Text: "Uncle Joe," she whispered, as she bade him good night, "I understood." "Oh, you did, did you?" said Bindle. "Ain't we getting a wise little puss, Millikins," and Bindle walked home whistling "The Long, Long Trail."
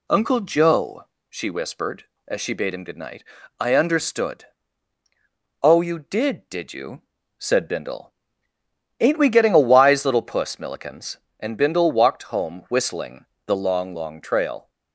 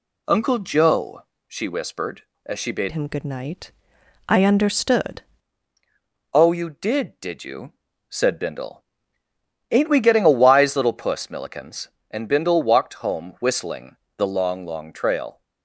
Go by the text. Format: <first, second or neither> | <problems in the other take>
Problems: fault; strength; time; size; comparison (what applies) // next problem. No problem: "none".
first | changes voice from "him" to "understood"; from 2.9 to 5.2 s; 2.3 s long // pauses between "whistling" and "The"; slight; at 13.9 s; 0.20 s long; slight in the first